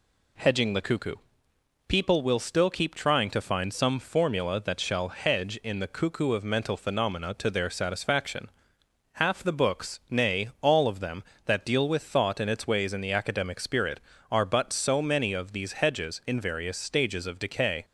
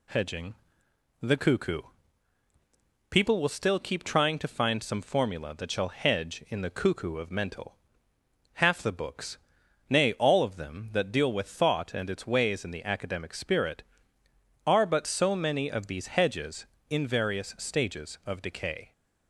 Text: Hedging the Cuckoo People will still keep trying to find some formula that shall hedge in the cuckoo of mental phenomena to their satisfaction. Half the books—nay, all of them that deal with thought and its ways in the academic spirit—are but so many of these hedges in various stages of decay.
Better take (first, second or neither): first